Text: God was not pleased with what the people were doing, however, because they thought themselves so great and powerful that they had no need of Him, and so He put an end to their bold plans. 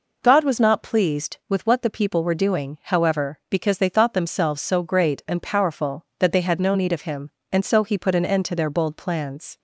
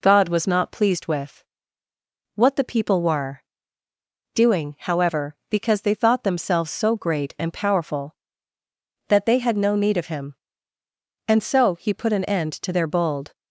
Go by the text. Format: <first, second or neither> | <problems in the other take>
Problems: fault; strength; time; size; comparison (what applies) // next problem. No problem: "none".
first | pauses between "with" and "what"; noticeable; at 1.4 s; 0.92 s long // pauses between "were" and "doing"; noticeable; at 3.4 s; 0.92 s long // stops before "plans"; at 13.3 s